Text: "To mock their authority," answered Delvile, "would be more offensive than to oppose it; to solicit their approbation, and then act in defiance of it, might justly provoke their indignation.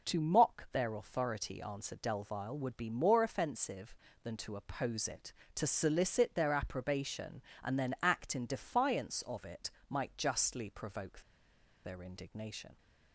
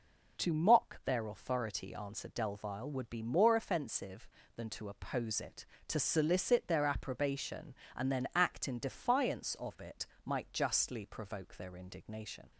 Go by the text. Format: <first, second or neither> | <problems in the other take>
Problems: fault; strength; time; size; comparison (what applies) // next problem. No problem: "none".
second | pauses between "provoke" and "their"; noticeable; at 11.2 s; 0.63 s long